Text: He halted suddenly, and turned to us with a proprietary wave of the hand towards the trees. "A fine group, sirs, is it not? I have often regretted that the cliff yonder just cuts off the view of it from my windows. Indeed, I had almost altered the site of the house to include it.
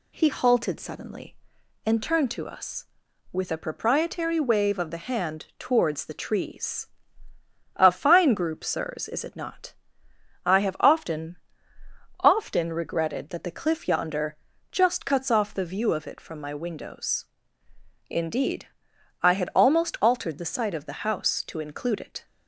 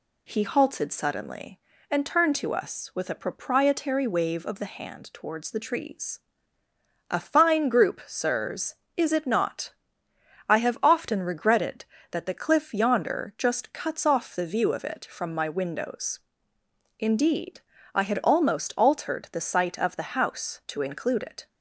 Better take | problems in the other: second | says "often" twice; at 12.1 s // pauses between "yonder" and "just"; slight; at 14.3 s; 0.34 s long

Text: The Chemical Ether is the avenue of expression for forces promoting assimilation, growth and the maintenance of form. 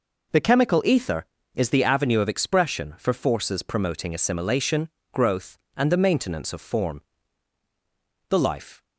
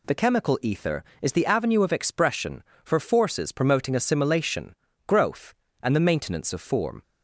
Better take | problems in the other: second | goes on to say "The Life"; from 8.2 s on; 0.54 s long

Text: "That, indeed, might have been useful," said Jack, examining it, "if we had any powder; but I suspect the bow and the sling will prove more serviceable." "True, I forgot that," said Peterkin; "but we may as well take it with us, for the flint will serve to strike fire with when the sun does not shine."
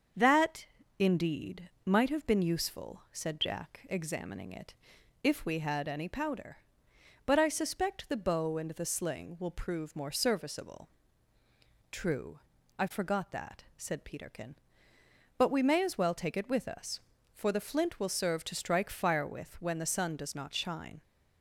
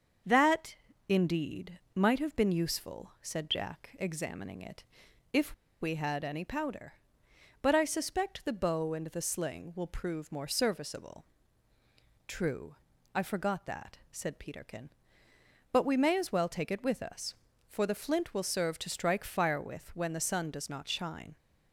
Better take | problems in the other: first | starts louder than the rest; until 1.5 s; 7 dB; also in the first // pauses between "if" and "we"; slight; at 5.5 s; 0.27 s long

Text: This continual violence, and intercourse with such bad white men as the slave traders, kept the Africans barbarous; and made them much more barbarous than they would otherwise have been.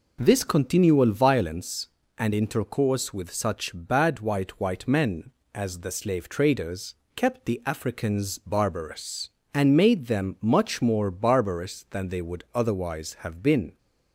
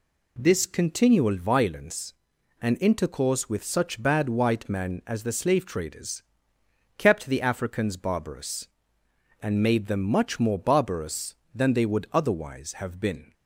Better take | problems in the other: second | says "white" twice; at 4.5 s

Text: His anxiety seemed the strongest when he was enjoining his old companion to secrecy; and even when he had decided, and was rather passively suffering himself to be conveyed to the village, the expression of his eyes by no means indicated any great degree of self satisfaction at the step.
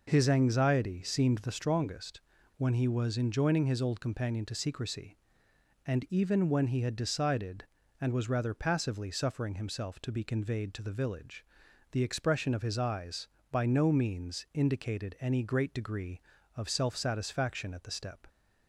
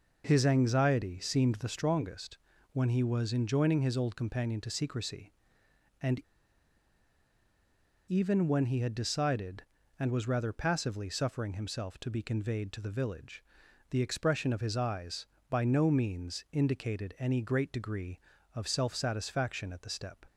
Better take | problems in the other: first | pauses between "strongest" and "when"; slight; at 2.3 s; 0.34 s long; slight in the first // pauses between "and" and "even"; strong; at 6.1 s; 1.8 s long

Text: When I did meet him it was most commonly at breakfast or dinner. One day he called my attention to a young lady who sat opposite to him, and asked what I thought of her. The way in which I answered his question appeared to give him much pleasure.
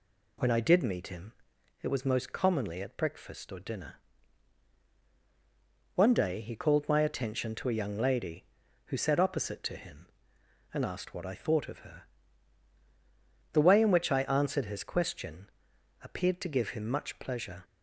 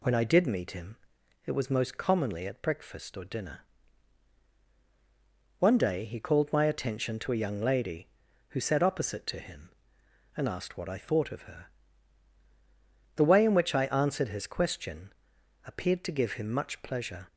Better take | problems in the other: neither | pauses between "him" and "it"; noticeable; the same in both // pauses between "question" and "appeared"; noticeable; the same in both

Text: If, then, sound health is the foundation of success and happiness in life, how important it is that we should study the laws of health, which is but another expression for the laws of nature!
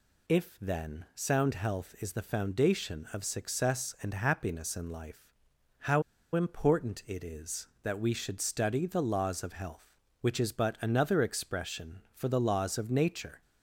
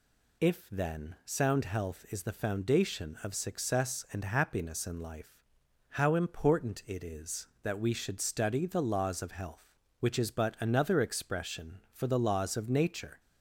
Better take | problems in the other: second | pauses between "how" and "important"; slight; at 6.0 s; 0.32 s long

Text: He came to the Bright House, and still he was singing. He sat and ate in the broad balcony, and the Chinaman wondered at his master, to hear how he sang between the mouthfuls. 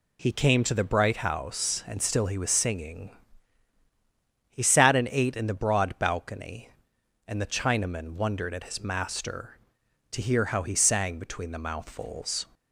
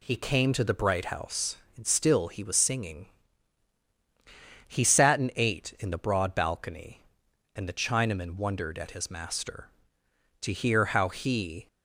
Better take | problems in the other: first | stops before "sang between the mouthfuls"; at 11.6 s

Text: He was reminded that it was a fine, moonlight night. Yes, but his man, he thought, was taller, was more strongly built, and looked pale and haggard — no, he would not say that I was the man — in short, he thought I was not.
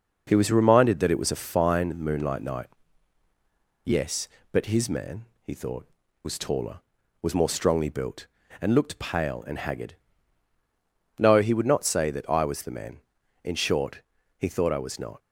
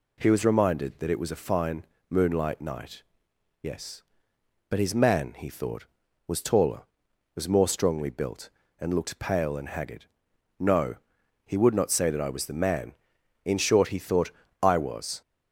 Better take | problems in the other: first | pauses between "thought" and "I"; slight; at 14.3 s; 0.30 s long // stops before "not"; at 15.2 s

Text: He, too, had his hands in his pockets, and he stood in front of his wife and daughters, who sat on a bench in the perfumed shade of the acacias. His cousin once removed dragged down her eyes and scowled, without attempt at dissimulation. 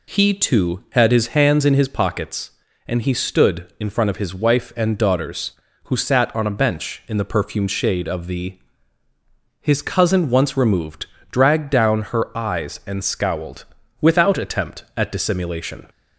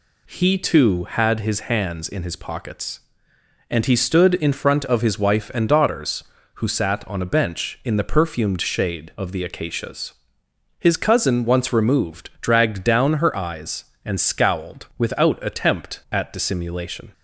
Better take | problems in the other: second | skips "acacias"; at 9.0 s // pauses between "removed" and "dragged"; slight; at 11.0 s; 0.22 s long

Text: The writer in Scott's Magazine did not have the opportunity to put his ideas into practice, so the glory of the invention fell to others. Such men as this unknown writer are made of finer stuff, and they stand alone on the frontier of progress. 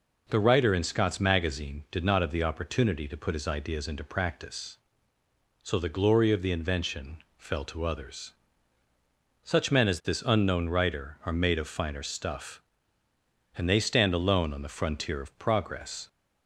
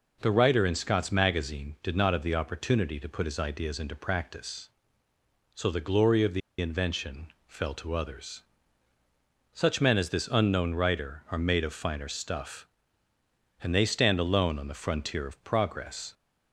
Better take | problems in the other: first | pauses between "the" and "invention"; slight; at 6.4 s; 0.20 s long // pauses between "invention" and "fell"; slight; at 7.2 s; 0.18 s long; slight in the first

